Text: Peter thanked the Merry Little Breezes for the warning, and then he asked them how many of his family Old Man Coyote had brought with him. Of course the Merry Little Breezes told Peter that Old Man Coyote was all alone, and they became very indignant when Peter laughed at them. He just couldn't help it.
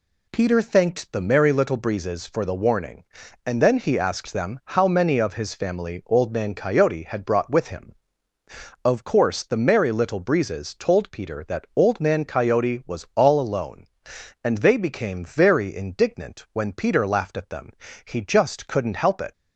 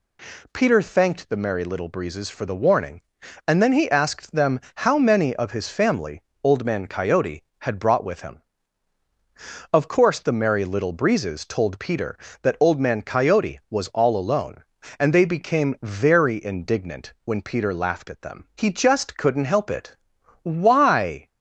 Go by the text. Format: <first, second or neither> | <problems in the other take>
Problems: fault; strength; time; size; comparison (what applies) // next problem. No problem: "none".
first | pauses between "family" and "Old"; slight; at 6.2 s; 0.24 s long // goes on to say "Why"; noticeable; from 20.4 s on; 0.86 s long